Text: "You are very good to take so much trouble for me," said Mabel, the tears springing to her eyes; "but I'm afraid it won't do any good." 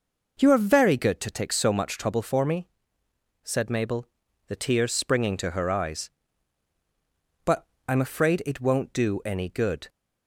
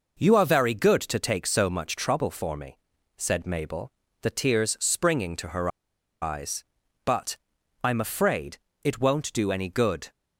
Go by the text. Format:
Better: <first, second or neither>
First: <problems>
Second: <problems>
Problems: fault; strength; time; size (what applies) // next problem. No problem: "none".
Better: first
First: pauses between "but" and "I'm"; slight; at 7.6 s; 0.22 s long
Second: pauses between "her" and "eyes"; noticeable; at 5.6 s; 0.52 s long // pauses between "but" and "I'm"; noticeable; at 7.3 s; 0.46 s long // pauses between "afraid" and "it"; slight; at 8.5 s; 0.24 s long